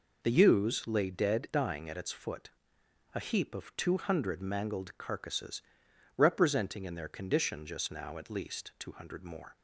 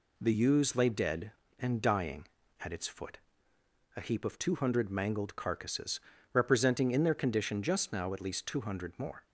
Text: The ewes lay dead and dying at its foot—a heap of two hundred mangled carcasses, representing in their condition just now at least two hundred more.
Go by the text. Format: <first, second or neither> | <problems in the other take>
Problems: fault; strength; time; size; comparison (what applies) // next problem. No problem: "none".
second | skips "and"; at 1.4 s